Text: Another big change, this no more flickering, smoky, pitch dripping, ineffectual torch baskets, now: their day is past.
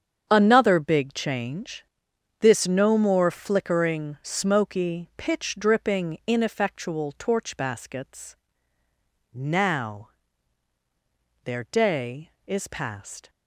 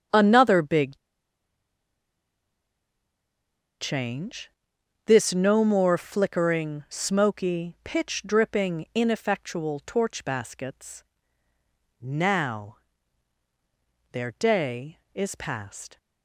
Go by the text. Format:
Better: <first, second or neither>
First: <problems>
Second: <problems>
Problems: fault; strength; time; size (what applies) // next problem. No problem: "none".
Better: first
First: starts louder than the rest; strong; until 1.3 s; 8 dB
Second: starts louder than the rest; strong; until 3.9 s; 8 dB // pauses between "big" and "change"; strong; at 0.9 s; 2.8 s long